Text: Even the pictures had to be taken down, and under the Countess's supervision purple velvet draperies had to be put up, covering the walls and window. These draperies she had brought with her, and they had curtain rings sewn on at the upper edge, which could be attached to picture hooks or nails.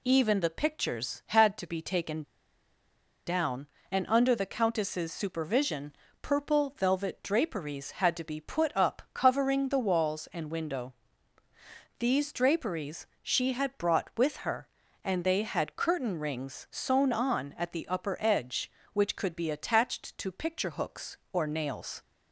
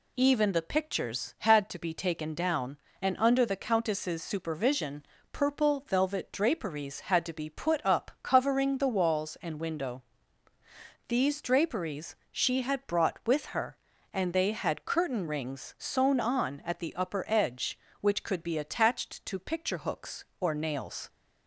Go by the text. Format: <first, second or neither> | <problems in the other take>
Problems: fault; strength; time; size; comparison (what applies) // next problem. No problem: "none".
second | pauses between "taken" and "down"; at 2.2 s; 1.0 s long // pauses between "supervision" and "purple"; slight; at 5.9 s; 0.28 s long; slight in the second // pauses between "draperies" and "she"; slight; at 13.0 s; 0.18 s long; slight in the second